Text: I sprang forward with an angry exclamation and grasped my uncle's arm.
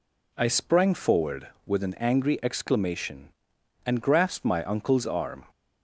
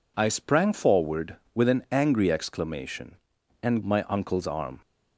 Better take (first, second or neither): first